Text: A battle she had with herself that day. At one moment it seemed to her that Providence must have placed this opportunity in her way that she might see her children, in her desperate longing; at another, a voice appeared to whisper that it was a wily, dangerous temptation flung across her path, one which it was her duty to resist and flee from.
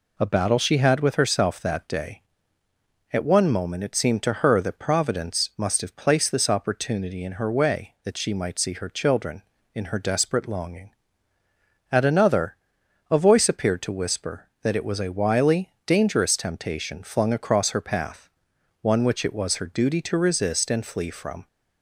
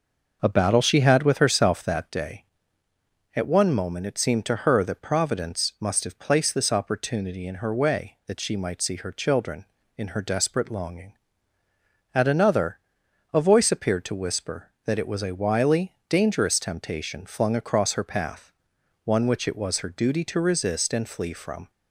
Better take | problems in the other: first | starts louder than the rest; noticeable; until 2.1 s; 6 dB

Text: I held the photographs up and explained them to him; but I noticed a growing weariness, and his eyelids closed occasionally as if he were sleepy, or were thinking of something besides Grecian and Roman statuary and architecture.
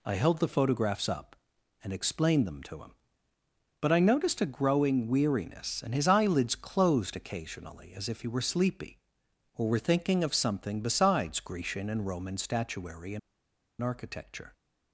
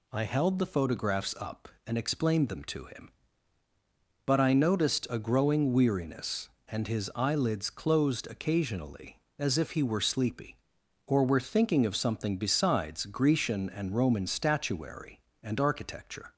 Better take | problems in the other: second | pauses between "and" and "architecture"; noticeable; at 13.1 s; 0.61 s long

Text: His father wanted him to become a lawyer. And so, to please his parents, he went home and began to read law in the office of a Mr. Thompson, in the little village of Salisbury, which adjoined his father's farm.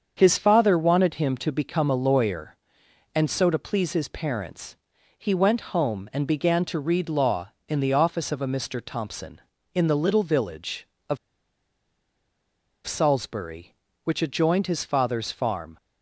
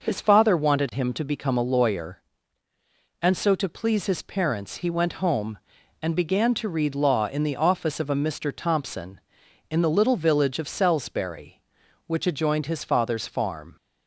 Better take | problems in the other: second | starts louder than the rest; until 1.1 s; 7 dB // pauses between "of" and "Salisbury"; strong; at 11.1 s; 1.6 s long

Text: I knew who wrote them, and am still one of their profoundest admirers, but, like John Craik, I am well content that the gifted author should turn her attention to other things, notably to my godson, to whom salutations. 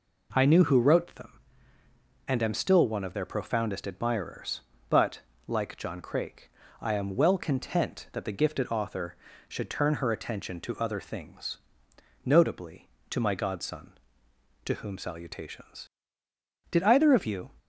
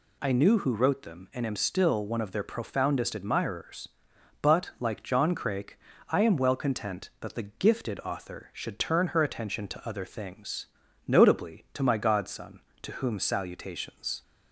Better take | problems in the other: second | goes on to say "Did either of you"; noticeable; from 16.6 s on; 0.82 s long

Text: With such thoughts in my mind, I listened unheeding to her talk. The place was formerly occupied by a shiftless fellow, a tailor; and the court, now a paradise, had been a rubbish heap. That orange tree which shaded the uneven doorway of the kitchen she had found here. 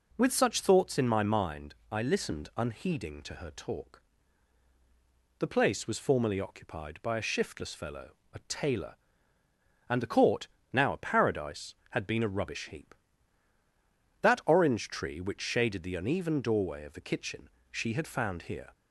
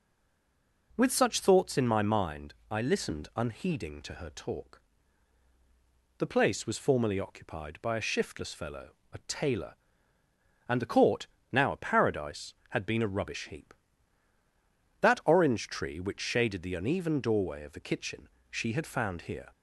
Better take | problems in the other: first | stays silent before the first word; slight; until 0.9 s; 0.9 s long // pauses between "kitchen" and "she"; slight; at 18.2 s; 0.22 s long; slight in the first

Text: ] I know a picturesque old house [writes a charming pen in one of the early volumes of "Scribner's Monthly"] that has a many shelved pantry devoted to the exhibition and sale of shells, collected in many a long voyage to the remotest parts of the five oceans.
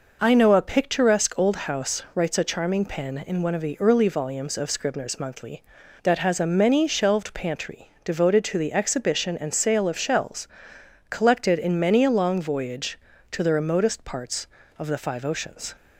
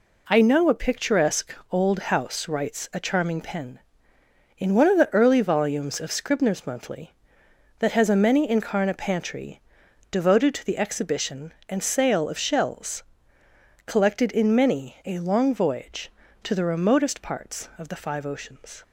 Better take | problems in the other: first | pauses between "picturesque" and "old"; slight; at 1.5 s; 0.16 s long // says "incarna" for "shelved"; at 8.4 s // pauses between "pantry" and "devoted"; noticeable; at 9.6 s; 0.50 s long; slight in the first

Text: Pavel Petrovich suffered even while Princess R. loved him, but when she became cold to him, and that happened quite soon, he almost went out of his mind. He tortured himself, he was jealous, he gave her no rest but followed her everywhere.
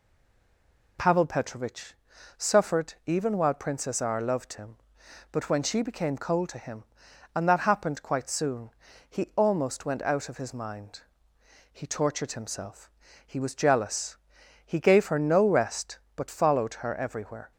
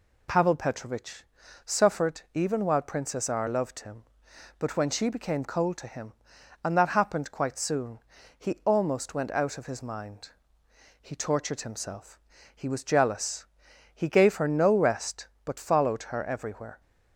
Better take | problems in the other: second | stays silent before the first word; slight; until 0.9 s; 0.9 s long // pauses between "Petrovich" and "suffered"; at 1.9 s; 0.42 s long; also in the second

